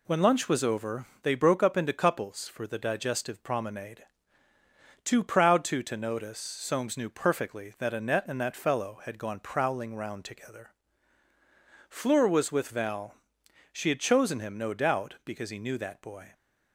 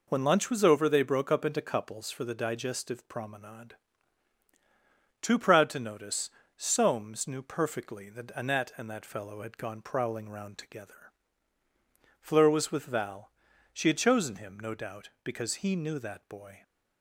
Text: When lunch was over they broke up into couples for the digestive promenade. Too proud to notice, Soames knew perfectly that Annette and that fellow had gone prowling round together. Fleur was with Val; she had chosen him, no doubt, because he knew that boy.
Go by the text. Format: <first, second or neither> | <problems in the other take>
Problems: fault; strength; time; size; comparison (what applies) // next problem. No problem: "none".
second | pauses between "over" and "they"; slight; at 1.0 s; 0.16 s long // says "to" twice; at 5.8 s